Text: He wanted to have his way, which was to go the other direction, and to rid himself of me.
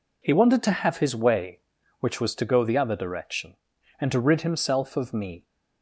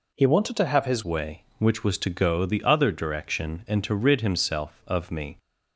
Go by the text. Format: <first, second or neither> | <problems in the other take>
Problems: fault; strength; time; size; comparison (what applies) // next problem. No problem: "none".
first | changes voice at "way"; from 1.0 s on; 4.3 s long